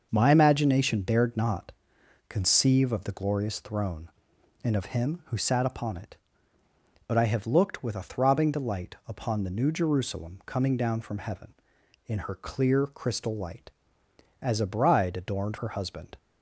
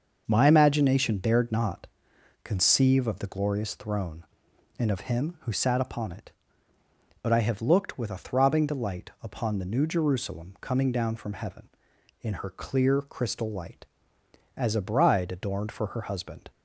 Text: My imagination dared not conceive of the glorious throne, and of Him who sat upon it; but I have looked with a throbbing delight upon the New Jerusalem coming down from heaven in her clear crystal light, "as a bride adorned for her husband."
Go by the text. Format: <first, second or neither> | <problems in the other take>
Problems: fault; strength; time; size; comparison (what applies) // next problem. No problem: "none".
second | starts louder than the rest; until 1.1 s; 6.5 dB; also in the second // pauses between "not" and "conceive"; noticeable; at 1.7 s; 0.58 s long; noticeable in the second // skips "for"; at 15.5 s